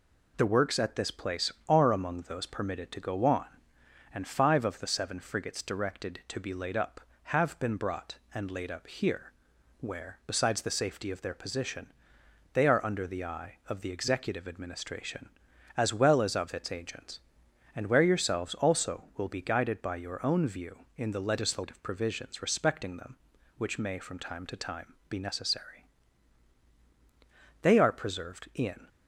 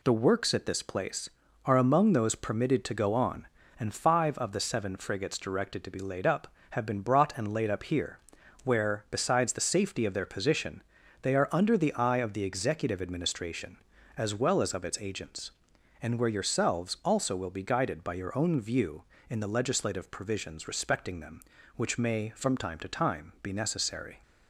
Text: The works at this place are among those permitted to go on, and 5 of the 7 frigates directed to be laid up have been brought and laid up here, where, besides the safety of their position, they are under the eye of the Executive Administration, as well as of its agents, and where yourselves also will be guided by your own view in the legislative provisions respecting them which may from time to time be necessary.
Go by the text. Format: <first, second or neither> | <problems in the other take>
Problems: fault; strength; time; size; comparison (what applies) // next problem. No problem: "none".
second | goes on to say "They are preserved in"; noticeable; from 27.6 s on; 1.2 s long